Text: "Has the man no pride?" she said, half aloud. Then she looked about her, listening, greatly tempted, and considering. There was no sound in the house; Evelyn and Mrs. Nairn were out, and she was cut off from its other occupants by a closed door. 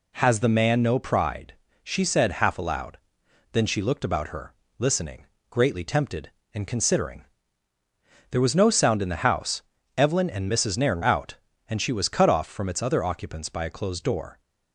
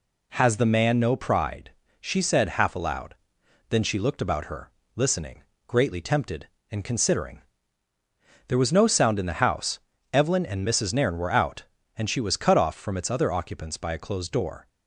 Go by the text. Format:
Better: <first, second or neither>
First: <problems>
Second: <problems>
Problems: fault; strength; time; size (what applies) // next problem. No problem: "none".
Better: second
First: skips "were"; at 11.0 s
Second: none